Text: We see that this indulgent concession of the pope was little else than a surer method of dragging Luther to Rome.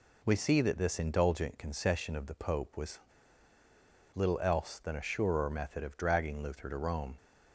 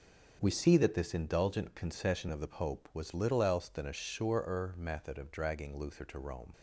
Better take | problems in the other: second | pauses between "was" and "little"; at 2.9 s; 1.1 s long

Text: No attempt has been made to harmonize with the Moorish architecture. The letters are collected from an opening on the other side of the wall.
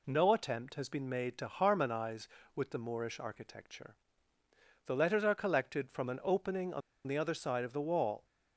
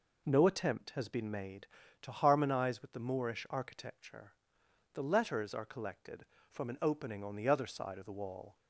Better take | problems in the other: second | pauses between "on" and "the"; slight; at 6.8 s; 0.25 s long

